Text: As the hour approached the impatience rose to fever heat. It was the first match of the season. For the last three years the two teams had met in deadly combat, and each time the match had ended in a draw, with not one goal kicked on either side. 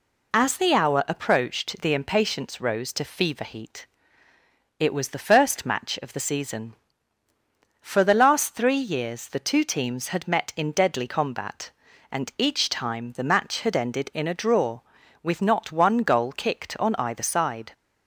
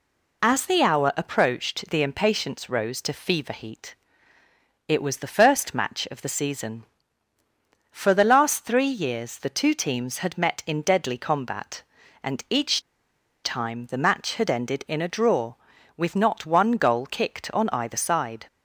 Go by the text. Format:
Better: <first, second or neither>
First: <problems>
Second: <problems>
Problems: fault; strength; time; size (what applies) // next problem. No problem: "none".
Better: first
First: none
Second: pauses between "each" and "time"; noticeable; at 12.8 s; 0.63 s long